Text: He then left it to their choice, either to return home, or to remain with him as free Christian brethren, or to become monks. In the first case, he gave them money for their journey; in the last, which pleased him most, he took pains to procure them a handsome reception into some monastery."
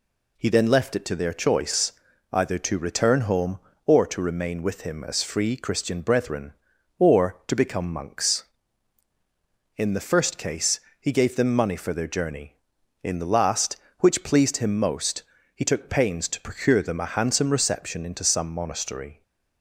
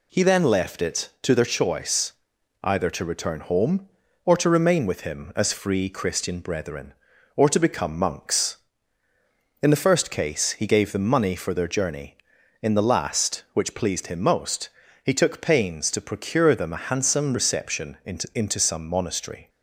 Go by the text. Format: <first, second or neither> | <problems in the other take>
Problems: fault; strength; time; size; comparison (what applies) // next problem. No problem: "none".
first | says "into" twice; at 18.3 s